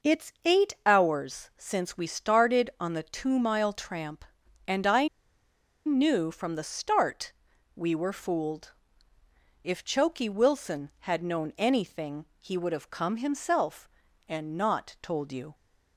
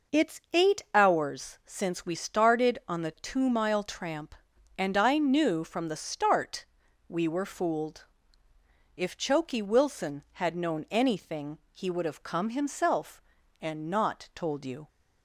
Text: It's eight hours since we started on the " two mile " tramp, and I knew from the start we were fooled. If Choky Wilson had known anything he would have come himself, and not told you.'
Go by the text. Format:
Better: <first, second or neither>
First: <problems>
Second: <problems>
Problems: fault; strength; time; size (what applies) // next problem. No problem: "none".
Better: second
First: pauses between "I" and "knew"; noticeable; at 5.0 s; 0.78 s long // pauses between "start" and "we"; at 7.3 s; 0.42 s long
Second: pauses between "start" and "we"; at 6.6 s; 0.42 s long